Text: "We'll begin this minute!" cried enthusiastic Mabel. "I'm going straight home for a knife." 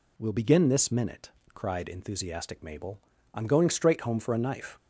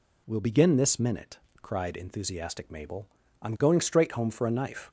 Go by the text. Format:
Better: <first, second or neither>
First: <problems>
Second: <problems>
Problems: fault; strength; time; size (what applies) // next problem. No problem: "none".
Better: neither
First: none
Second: none